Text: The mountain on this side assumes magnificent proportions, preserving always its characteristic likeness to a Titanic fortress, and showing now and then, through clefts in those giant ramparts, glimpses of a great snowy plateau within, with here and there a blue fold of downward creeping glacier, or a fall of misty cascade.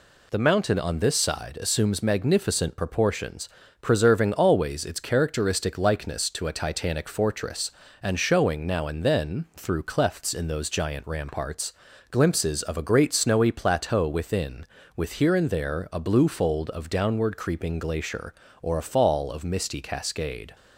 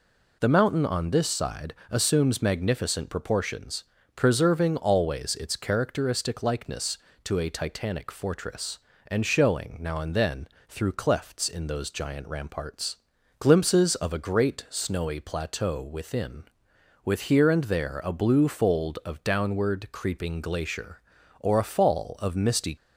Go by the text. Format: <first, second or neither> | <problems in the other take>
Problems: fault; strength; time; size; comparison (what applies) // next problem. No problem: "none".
first | pauses between "side" and "assumes"; slight; at 1.7 s; 0.18 s long // stops before "cascade"; at 22.7 s